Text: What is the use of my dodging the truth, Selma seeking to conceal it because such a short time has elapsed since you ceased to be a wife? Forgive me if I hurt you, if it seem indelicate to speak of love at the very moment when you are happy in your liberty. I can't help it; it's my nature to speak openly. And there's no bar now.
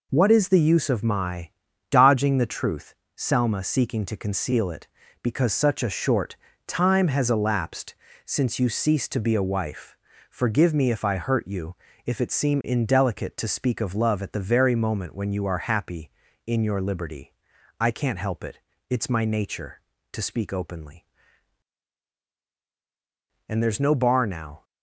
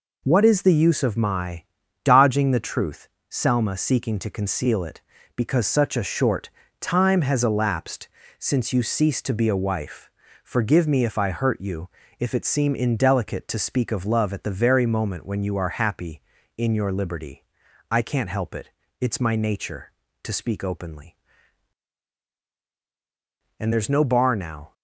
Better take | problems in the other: neither | pauses between "my" and "dodging"; the same in both // pauses between "short" and "time"; slight; the same in both // pauses between "elapsed" and "since"; slight; the same in both

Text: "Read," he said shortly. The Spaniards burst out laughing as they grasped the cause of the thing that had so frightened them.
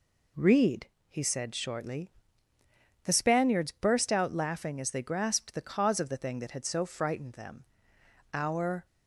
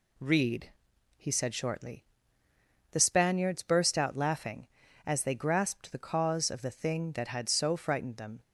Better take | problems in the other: second | goes on to say "Our"; from 8.3 s on; 0.52 s long

